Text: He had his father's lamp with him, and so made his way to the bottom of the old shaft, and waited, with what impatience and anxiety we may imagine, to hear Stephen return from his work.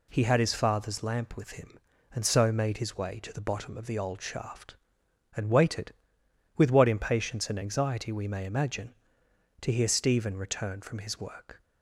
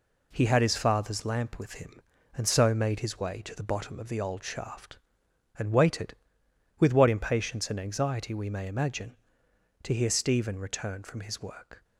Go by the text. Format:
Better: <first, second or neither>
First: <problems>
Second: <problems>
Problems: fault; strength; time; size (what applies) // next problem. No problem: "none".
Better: first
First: none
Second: gets quieter; noticeable; throughout; 6 dB